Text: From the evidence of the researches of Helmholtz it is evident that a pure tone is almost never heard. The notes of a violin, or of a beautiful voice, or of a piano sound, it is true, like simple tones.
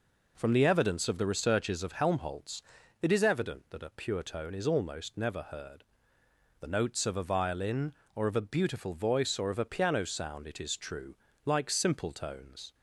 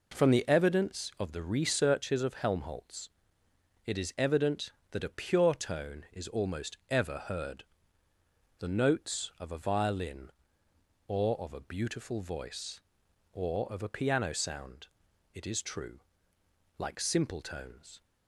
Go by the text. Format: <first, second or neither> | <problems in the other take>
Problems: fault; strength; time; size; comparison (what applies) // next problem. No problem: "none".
first | pauses between "Helmholtz" and "it"; noticeable; at 3.0 s; 0.78 s long; also in the first // says "ever" for "never"; at 6.9 s